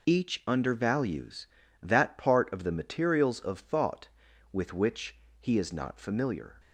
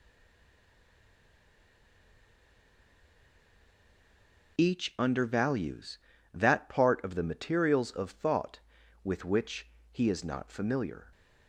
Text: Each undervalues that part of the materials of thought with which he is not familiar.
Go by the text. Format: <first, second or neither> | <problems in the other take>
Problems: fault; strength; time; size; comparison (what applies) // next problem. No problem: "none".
first | stays silent before the first word; strong; until 4.5 s; 4.5 s long // pauses between "which" and "he"; slight; at 9.6 s; 0.24 s long; slight in the first